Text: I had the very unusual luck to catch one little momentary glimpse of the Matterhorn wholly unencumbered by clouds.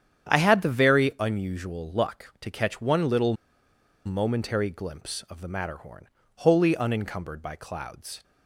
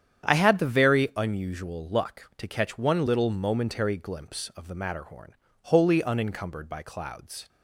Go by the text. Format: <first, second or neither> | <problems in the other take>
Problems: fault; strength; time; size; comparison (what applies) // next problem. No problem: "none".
second | starts louder than the rest; strong; until 1.3 s; 9 dB; strong in the second // pauses between "little" and "momentary"; noticeable; at 3.3 s; 0.72 s long // pauses between "Matterhorn" and "wholly"; slight; at 6.0 s; 0.28 s long; slight in the second